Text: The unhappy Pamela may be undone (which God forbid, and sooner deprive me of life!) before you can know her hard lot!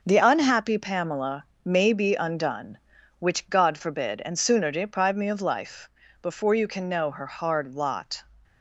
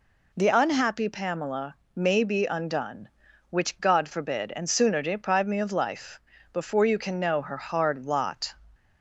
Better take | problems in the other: second | gets quieter; throughout; 6.5 dB // pauses between "Pamela" and "may"; slight; at 1.4 s; 0.18 s long; slight in the second

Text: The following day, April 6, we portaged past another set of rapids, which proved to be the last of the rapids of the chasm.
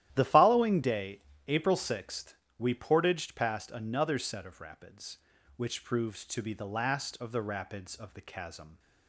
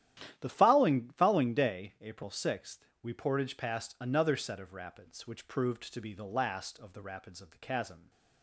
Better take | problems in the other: first | starts louder than the rest; strong; until 1.4 s; 11.5 dB; strong in the first // says "following" twice; at 1.1 s

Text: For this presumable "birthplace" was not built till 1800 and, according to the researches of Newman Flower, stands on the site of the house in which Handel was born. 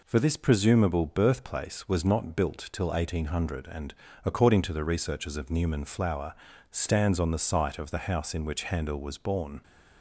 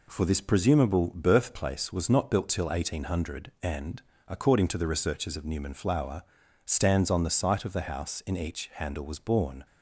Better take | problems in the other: first | says "each" for "which"; at 8.3 s

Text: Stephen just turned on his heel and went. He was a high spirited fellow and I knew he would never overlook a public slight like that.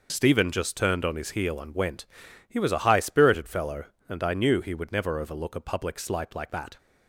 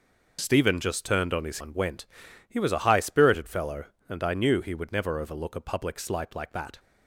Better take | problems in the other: first | skips "heel"; at 1.5 s

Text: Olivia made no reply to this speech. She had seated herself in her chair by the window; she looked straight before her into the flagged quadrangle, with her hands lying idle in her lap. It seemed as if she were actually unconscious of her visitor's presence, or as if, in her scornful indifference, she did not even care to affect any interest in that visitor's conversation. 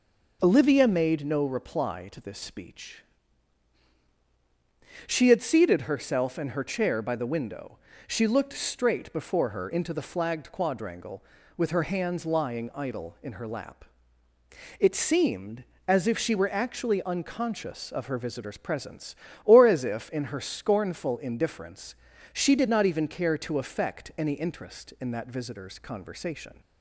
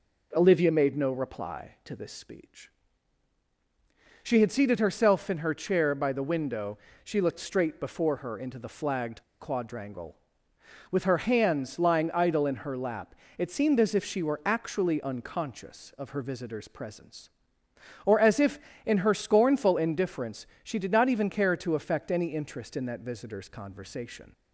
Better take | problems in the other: first | pauses between "flagged" and "quadrangle"; slight; at 9.2 s; 0.18 s long

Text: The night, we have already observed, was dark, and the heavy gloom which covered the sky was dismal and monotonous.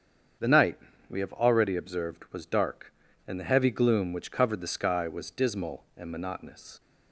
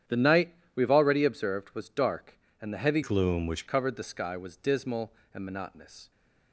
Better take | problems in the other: first | starts louder than the rest; strong; until 1.3 s; 10 dB; strong in the first // changes voice from "gloom" to "which"; from 3.0 to 3.6 s; 0.6 s long

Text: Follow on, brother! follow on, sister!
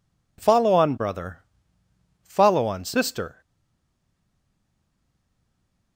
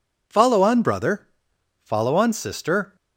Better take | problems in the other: second | stays silent after the last word; strong; from 3.4 s on; 2.5 s long

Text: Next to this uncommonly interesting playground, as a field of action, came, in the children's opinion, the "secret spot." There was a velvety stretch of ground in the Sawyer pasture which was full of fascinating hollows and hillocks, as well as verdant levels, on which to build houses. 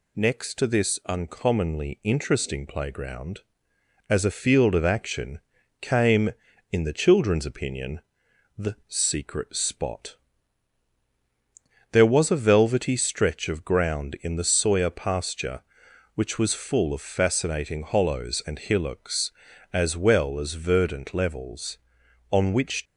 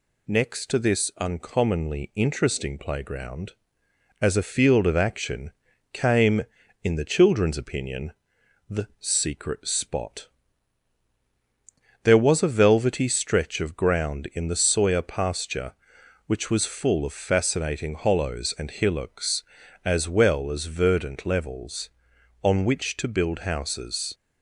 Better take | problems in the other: second | stops before "to build houses"; at 22.8 s

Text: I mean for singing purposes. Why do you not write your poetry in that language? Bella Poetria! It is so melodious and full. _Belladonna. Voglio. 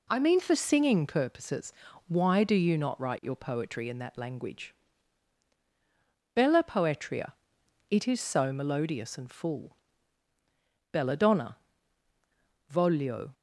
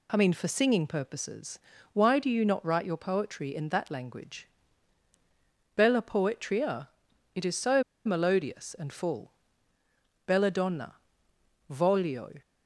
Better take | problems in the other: first | pauses between "so" and "melodious"; slight; at 7.8 s; 0.22 s long

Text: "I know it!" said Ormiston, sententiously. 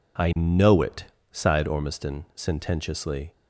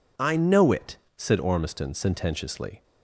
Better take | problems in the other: second | says "sighed" for "said"; at 1.3 s

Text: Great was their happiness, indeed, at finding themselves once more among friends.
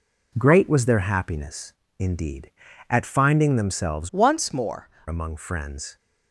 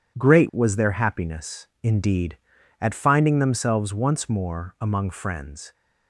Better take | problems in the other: second | changes voice from "once" to "more"; from 4.1 to 4.8 s; 0.7 s long

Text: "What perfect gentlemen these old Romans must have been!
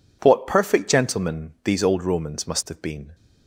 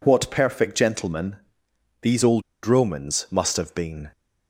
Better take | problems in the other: first | pauses between "gentlemen" and "these"; noticeable; at 1.3 s; 0.64 s long // pauses between "old" and "Romans"; slight; at 2.4 s; 0.23 s long

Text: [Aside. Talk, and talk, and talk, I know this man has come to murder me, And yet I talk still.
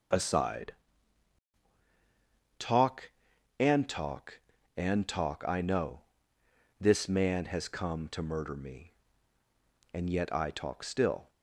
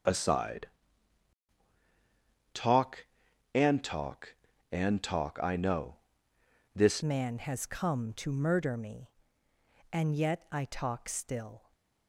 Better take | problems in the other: first | starts louder than the rest; until 2.9 s; 6.5 dB; noticeable in the first // pauses between "know" and "this"; noticeable; at 5.9 s; 0.80 s long; noticeable in the first // changes voice at "man"; from 7.0 s on; 4.7 s long // stays silent after the last word; slight; from 11.5 s on; 0.5 s long

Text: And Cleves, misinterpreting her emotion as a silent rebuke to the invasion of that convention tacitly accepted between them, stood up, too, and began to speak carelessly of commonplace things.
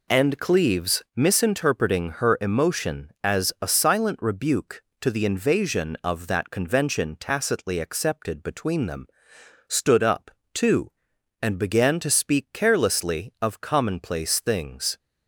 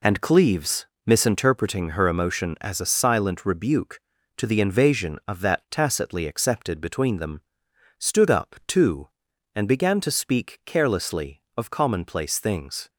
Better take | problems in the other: first | skips "convention"; at 5.6 s

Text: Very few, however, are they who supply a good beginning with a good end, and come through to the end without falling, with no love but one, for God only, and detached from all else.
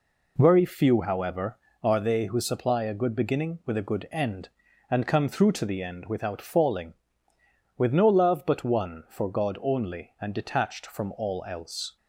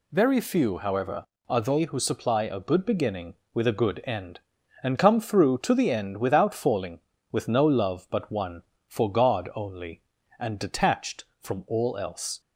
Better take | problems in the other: neither | none

